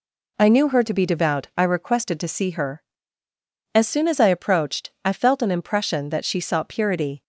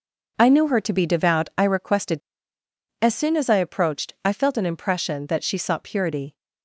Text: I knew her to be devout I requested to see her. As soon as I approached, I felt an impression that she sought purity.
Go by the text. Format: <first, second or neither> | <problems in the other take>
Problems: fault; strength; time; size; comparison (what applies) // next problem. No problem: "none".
first | skips "to see her"; at 2.6 s